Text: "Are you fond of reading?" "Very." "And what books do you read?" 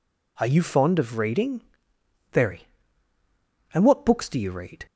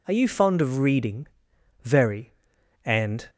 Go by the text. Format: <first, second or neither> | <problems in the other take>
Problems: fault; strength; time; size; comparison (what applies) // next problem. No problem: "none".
first | stops before "what books do you read"; at 3.2 s